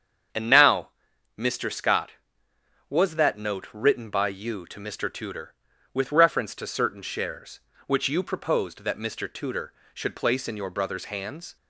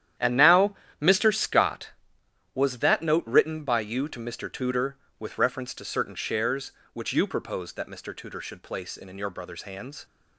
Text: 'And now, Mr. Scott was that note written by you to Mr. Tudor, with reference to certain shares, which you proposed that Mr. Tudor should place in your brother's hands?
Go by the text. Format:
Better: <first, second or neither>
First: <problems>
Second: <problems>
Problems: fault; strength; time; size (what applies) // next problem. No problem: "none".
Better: first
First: starts louder than the rest; strong; until 1.7 s; 7.5 dB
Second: starts louder than the rest; strong; until 1.4 s; 10.5 dB // says "in" twice; at 9.0 s